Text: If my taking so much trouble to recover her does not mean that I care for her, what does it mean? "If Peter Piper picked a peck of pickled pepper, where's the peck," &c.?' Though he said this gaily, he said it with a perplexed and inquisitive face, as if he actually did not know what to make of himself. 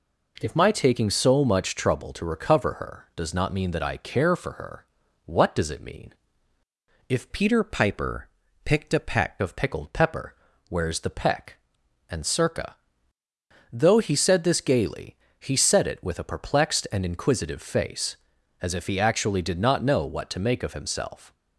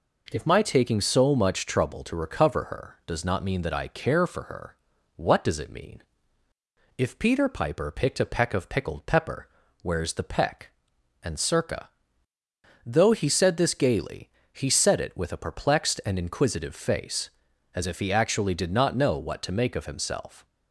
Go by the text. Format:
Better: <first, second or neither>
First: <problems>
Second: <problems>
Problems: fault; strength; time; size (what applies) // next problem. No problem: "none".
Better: second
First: changes voice from "Peter" to "peck"; from 7.3 to 9.4 s; 2.1 s long // pauses between "Piper" and "picked"; slight; at 8.2 s; 0.34 s long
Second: none